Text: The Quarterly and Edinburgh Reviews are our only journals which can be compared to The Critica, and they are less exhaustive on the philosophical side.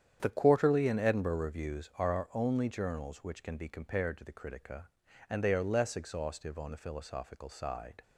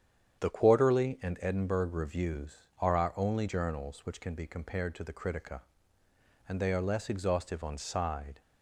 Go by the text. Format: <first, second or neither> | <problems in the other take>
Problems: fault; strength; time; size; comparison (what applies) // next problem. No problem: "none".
first | starts louder than the rest; strong; until 1.4 s; 8.5 dB; strong in the first // skips "the philosophical"; at 7.7 s